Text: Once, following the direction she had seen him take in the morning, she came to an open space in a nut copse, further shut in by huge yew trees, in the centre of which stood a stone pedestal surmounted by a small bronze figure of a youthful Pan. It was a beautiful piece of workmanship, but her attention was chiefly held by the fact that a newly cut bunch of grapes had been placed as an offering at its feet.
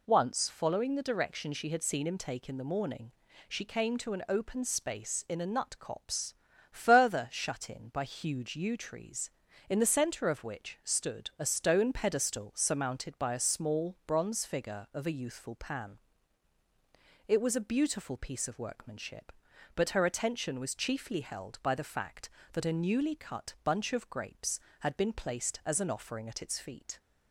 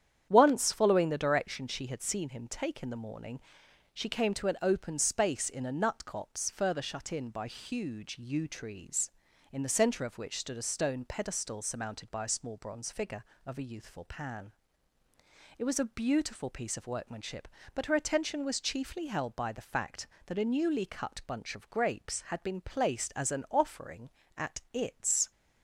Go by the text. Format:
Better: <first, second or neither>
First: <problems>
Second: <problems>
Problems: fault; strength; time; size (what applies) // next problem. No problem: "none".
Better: first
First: none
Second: starts louder than the rest; strong; until 1.3 s; 9.5 dB // stops before "feet"; at 25.3 s